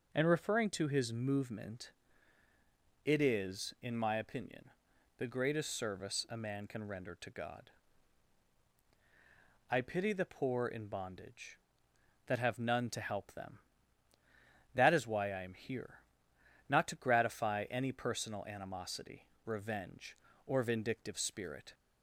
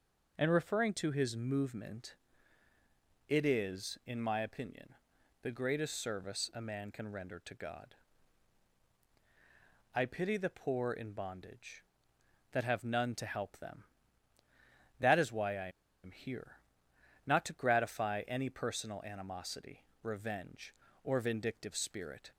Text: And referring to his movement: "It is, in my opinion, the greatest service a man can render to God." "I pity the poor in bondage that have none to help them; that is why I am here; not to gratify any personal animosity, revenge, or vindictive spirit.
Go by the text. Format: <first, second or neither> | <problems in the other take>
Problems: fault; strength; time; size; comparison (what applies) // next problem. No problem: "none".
first | pauses between "I" and "am"; slight; at 15.6 s; 0.34 s long